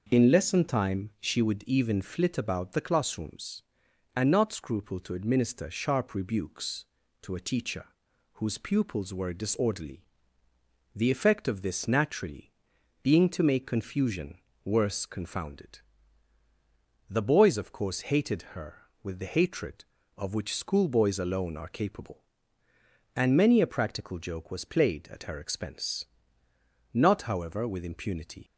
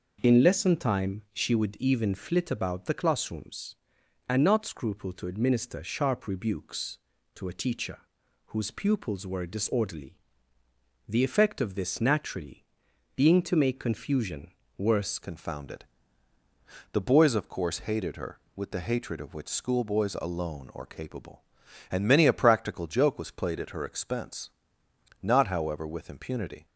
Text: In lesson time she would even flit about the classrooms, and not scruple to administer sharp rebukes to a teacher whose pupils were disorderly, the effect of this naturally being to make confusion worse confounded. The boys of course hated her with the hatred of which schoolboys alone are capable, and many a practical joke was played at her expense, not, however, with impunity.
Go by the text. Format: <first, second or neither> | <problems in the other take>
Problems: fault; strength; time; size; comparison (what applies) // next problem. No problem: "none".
first | pauses between "teacher" and "whose"; noticeable; at 7.9 s; 0.48 s long; noticeable in the first // pauses between "naturally" and "being"; noticeable; at 12.6 s; 0.50 s long; noticeable in the first // pauses between "confusion" and "worse"; slight; at 14.5 s; 0.26 s long; slight in the first // changes voice at "confounded"; from 15.2 s on; 11.4 s long